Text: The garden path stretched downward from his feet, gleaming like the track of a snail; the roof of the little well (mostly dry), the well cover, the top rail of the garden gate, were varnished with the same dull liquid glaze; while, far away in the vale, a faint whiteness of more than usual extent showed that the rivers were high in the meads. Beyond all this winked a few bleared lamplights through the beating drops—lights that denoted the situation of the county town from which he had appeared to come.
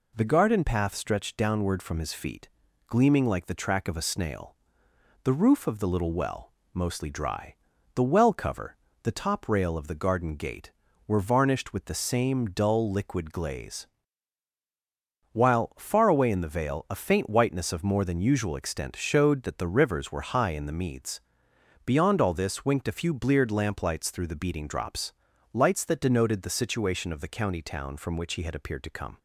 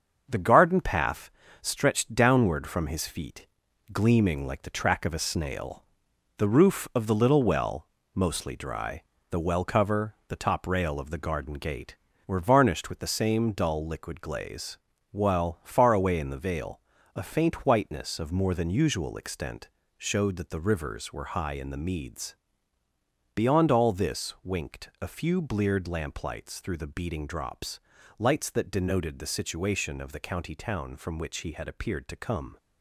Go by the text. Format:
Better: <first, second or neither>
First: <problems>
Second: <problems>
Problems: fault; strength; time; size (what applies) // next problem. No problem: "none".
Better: first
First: none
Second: gets quieter; throughout; 6.5 dB // pauses between "path" and "stretched"; slight; at 1.3 s; 0.30 s long // pauses between "extent" and "showed"; slight; at 19.6 s; 0.28 s long